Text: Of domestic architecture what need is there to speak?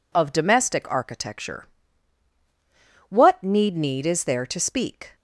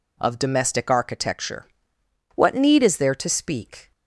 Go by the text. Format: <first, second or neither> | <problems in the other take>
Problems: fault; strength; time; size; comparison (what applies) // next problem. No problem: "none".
second | pauses between "architecture" and "what"; strong; at 1.6 s; 1.4 s long; noticeable in the second // says "need" twice; at 3.7 s